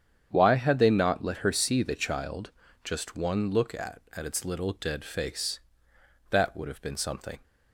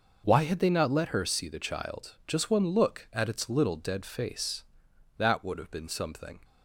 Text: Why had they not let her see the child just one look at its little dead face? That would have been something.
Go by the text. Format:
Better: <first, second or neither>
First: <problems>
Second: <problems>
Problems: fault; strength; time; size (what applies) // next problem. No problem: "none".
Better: second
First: starts louder than the rest; strong; until 1.3 s; 8.5 dB // pauses between "child" and "just"; slight; at 2.5 s; 0.34 s long // says "at" twice; at 4.1 s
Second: none